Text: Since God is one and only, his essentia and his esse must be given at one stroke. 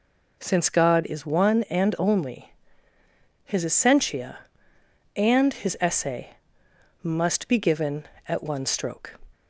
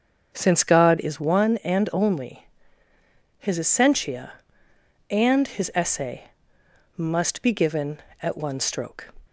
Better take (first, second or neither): first